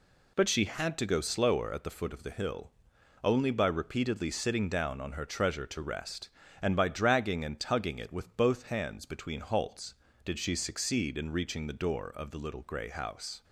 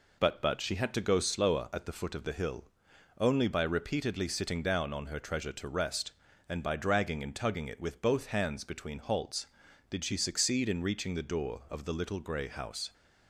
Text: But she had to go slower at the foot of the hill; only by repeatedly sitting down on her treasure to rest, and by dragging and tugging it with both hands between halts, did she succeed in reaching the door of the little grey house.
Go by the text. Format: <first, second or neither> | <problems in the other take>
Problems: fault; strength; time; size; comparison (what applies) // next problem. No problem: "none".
first | says "But" twice; at 0.4 s